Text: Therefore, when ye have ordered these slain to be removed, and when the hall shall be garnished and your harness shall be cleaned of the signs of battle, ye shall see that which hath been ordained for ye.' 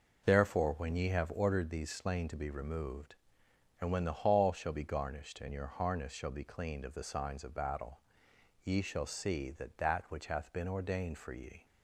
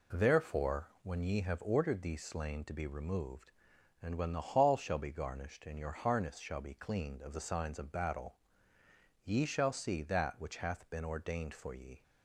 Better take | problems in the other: second | says "that" twice; at 9.7 s

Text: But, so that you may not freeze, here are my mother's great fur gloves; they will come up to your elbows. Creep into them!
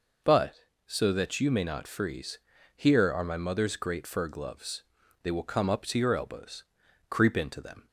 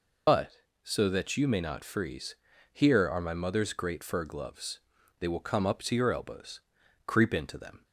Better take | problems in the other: first | loses the start of "But"; at 0.2 s; 70 ms

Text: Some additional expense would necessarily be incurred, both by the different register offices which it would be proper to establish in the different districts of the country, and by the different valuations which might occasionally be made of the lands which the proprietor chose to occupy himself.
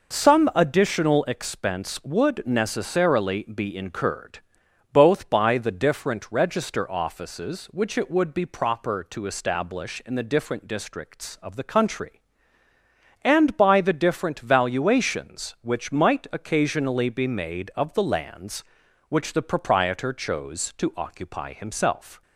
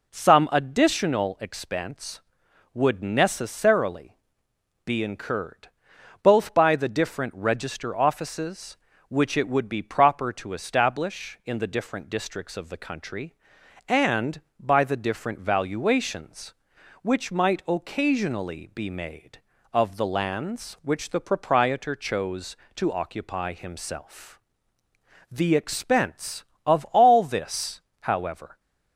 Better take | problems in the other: first | pauses between "necessarily" and "be"; noticeable; at 4.1 s; 0.68 s long // goes on to say "The expense of all this however"; strong; from 25.3 s on; 3.2 s long

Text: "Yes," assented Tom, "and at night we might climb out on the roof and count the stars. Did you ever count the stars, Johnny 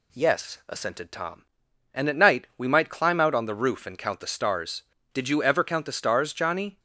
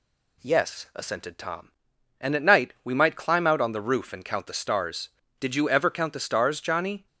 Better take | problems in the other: neither | none

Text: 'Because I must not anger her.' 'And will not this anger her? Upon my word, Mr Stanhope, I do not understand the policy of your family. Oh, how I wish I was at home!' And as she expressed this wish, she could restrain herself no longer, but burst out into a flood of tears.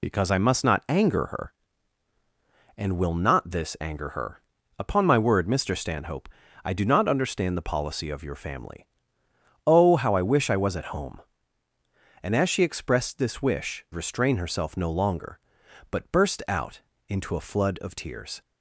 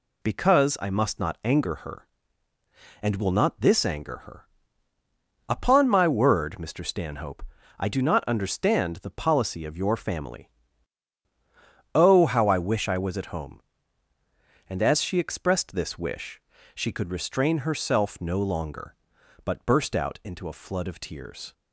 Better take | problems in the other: second | skips "she could"; at 13.9 s // pauses between "out" and "into"; slight; at 16.8 s; 0.26 s long

